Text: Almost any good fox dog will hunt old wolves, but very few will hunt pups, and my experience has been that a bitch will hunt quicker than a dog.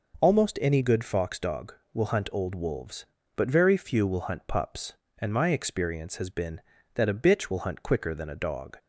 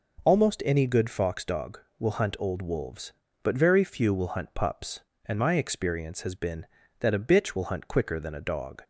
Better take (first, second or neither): neither